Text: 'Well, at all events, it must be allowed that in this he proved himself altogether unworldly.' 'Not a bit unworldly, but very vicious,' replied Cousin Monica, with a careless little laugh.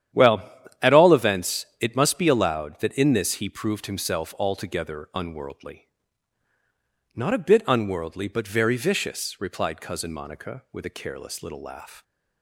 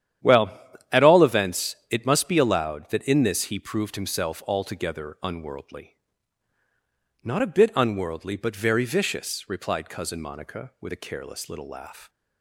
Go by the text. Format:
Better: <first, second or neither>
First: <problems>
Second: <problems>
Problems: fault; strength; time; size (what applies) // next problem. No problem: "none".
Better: neither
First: starts louder than the rest; strong; until 1.5 s; 10 dB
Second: starts louder than the rest; strong; until 1.6 s; 10 dB